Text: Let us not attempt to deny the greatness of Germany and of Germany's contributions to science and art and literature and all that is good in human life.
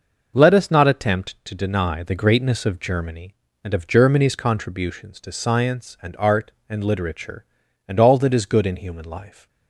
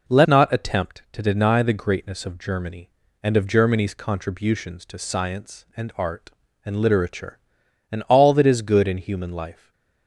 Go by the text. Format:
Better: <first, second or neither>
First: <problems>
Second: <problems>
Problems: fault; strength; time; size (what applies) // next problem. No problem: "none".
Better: first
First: none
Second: skips "us"; at 0.2 s // stays silent after the last word; slight; from 9.5 s on; 0.5 s long